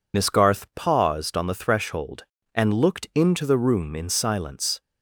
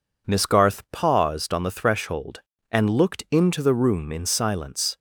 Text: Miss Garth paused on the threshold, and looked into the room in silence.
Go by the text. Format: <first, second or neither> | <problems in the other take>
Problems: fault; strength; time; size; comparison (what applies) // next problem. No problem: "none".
second | loses the start of "Miss"; at 0.1 s; 40 ms